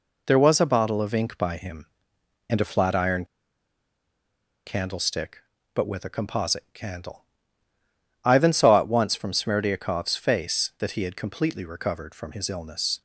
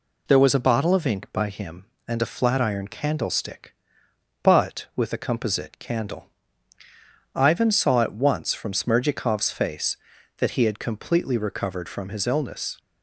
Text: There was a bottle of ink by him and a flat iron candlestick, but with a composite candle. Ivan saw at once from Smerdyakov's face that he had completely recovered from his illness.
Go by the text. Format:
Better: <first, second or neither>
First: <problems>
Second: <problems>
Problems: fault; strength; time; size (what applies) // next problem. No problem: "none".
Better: second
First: pauses between "iron" and "candlestick"; strong; at 3.2 s; 1.4 s long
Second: none